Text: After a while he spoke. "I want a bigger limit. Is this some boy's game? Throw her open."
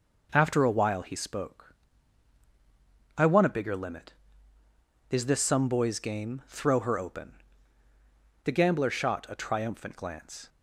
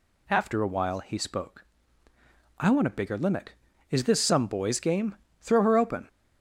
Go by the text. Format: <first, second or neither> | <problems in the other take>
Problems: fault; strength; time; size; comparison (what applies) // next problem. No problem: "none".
second | goes on to say "The gambler shot a triumphant glance"; strong; from 8.4 s on; 2.0 s long